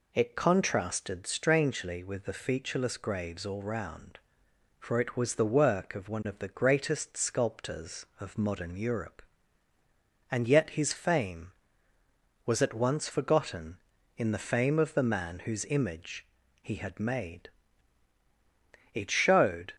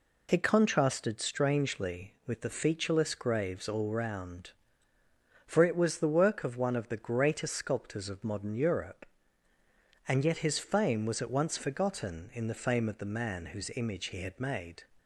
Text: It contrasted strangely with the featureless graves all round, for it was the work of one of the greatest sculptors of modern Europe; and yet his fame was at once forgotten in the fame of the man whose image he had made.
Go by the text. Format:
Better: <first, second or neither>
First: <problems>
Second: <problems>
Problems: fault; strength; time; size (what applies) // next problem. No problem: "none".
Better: second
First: pauses between "image" and "he"; slight; at 16.2 s; 0.34 s long // goes on to say "It showed"; noticeable; from 18.9 s on; 0.80 s long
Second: none